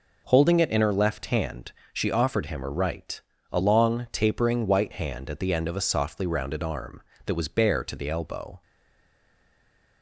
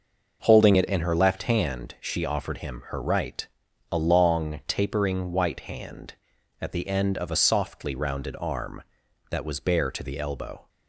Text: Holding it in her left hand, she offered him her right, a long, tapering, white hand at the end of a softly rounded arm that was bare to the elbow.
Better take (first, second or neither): second